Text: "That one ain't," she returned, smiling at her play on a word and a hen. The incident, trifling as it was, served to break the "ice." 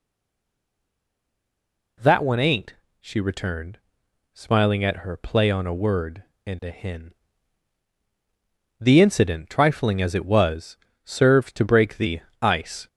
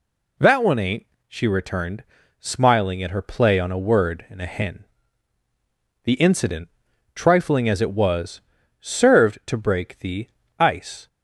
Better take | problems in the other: second | stays silent before the first word; noticeable; until 1.9 s; 1.9 s long // pauses between "the" and "ice"; slight; at 12.2 s; 0.20 s long; slight in the second

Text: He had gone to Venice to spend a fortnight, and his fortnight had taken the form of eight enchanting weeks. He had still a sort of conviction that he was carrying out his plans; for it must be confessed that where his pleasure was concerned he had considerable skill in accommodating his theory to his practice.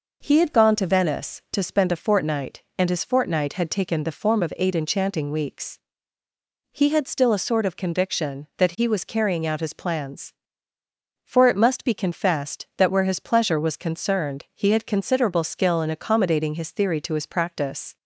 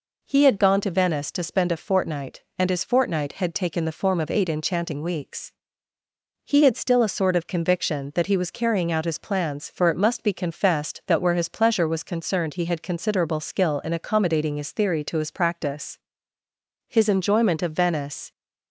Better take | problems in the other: first | goes on to say "His enjoyment of Venice"; from 16.8 s on; 1.4 s long

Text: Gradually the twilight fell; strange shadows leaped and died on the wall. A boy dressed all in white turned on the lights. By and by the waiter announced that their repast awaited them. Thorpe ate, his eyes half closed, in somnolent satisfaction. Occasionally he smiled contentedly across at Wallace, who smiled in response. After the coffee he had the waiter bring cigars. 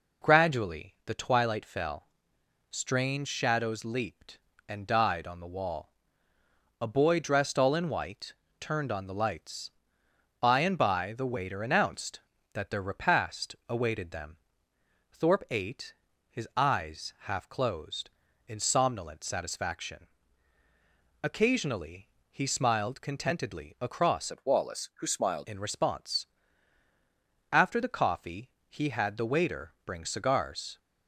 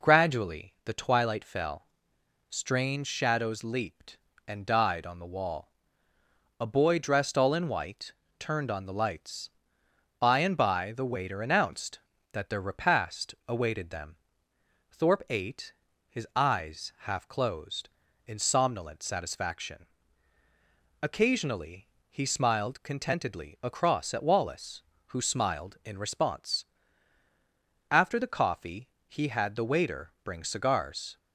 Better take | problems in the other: second | pauses between "white" and "turned"; slight; at 8.3 s; 0.28 s long; slight in the second // pauses between "Occasionally" and "he"; slight; at 22.0 s; 0.24 s long; slight in the second // changes voice from "at" to "smiled"; from 24.3 to 25.4 s; 1.1 s long // pauses between "coffee" and "he"; slight; at 28.4 s; 0.18 s long; slight in the second

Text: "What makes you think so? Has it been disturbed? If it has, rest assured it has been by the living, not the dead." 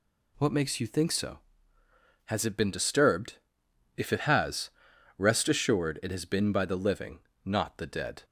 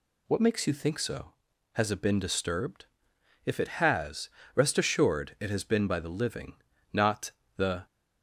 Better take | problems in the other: first | pauses between "not" and "the"; slight; at 7.3 s; 0.24 s long // stops before "dead"; at 7.8 s

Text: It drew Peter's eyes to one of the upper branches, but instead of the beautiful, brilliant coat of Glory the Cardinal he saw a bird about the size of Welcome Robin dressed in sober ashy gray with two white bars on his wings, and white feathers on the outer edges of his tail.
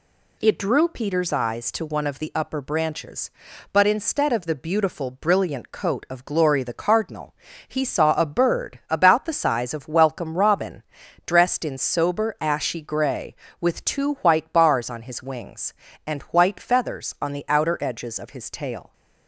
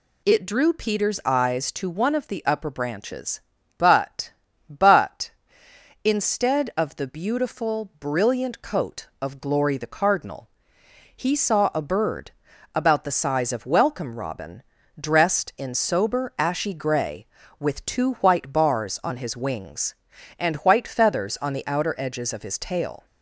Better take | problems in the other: first | says "but" twice; at 4.6 s // pauses between "Cardinal" and "he"; noticeable; at 10.4 s; 0.68 s long; slight in the first // pauses between "bird" and "about"; noticeable; at 12.2 s; 0.46 s long // pauses between "Robin" and "dressed"; at 14.6 s; 0.38 s long; also in the first

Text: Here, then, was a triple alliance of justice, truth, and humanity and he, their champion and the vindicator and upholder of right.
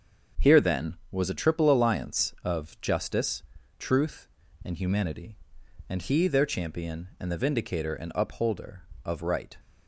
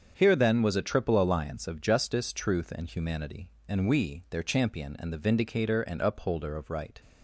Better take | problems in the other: first | starts louder than the rest; until 1.1 s; 7 dB; also in the first // says "we" for "he"; at 3.8 s

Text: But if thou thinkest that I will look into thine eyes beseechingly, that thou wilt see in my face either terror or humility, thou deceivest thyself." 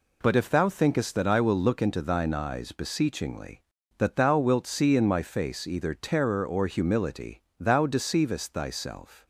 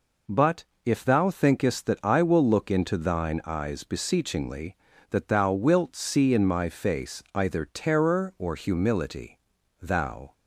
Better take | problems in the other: first | pauses between "But" and "if"; slight; at 0.6 s; 0.22 s long // stops before "deceivest thyself"; at 10.3 s

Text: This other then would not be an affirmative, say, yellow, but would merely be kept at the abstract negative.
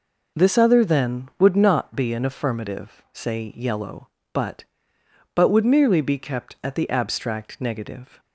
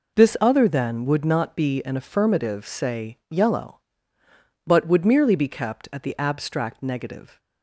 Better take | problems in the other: second | says "but" twice; at 5.3 s

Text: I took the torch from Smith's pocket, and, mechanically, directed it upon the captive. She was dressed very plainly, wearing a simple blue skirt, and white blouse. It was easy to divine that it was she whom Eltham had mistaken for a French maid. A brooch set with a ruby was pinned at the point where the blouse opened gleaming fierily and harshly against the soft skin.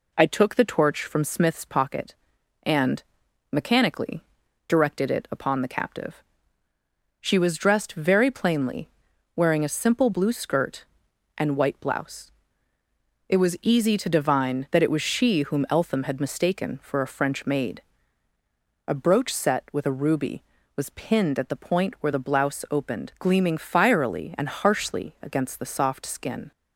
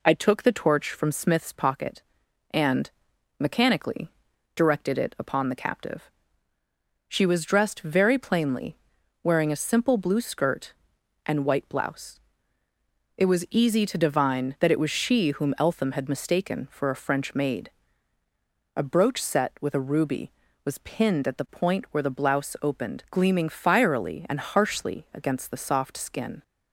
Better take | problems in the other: neither | none

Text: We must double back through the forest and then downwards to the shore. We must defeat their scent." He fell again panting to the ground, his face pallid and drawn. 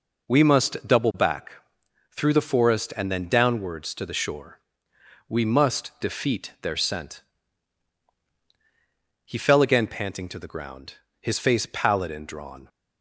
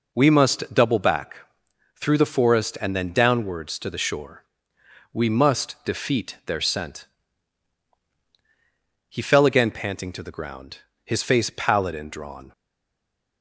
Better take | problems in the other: first | pauses between "back" and "through"; noticeable; at 1.3 s; 0.58 s long; noticeable in the first // stays silent after the last word; slight; from 12.5 s on; 0.9 s long

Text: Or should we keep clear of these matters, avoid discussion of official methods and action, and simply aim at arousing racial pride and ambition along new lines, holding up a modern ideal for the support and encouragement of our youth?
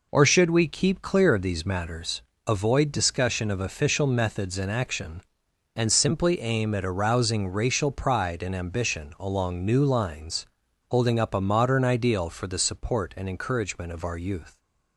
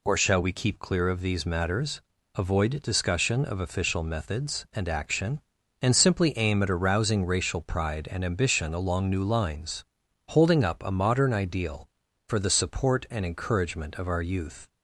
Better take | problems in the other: first | says "shall" for "should"; at 0.1 s

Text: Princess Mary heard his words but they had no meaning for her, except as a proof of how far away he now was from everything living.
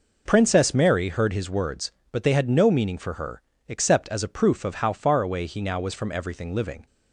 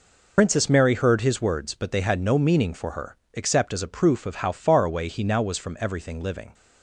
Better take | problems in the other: first | loses the start of "Princess"; at 0.3 s; 80 ms

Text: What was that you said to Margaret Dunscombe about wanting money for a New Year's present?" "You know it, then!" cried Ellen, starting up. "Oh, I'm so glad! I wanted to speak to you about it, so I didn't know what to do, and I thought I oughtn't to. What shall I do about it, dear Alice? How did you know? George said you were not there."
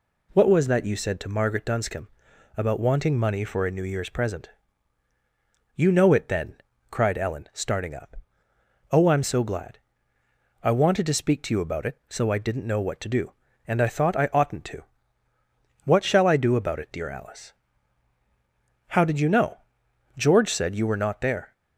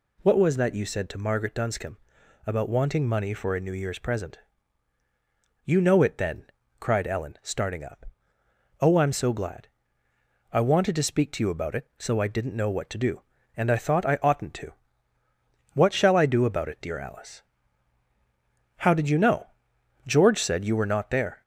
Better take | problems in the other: first | gets louder; slight; throughout; 2.5 dB // pauses between "Dunscombe" and "about"; noticeable; at 1.9 s; 0.50 s long; noticeable in the first

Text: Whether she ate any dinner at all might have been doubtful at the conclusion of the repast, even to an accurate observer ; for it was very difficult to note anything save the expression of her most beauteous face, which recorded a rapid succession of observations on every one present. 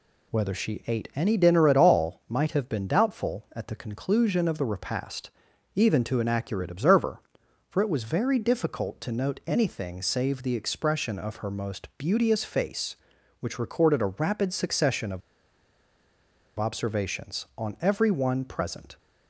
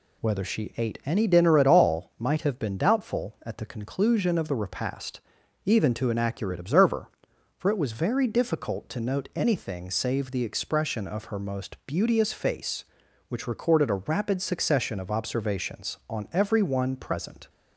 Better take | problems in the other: second | pauses between "of" and "observations"; strong; at 15.2 s; 1.3 s long

